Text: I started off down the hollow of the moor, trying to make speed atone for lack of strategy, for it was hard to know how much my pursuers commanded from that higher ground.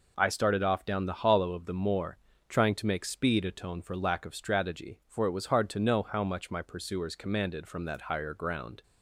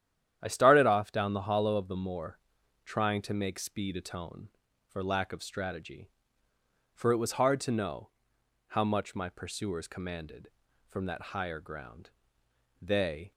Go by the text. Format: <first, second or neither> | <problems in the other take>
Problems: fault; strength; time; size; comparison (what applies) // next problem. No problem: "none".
first | starts louder than the rest; strong; until 1.4 s; 10 dB // pauses between "know" and "how"; noticeable; at 8.0 s; 0.58 s long // goes on to say "They"; from 12.8 s on; 0.50 s long